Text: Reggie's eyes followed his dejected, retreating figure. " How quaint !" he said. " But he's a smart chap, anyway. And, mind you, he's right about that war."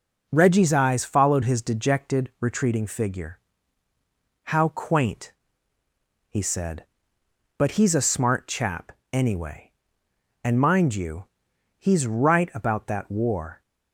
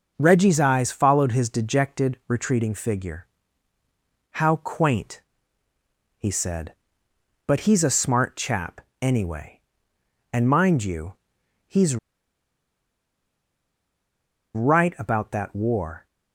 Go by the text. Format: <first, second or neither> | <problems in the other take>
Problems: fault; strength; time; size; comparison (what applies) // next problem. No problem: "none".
first | starts louder than the rest; until 1.1 s; 7 dB; also in the first // pauses between "he's" and "right"; strong; at 11.9 s; 2.5 s long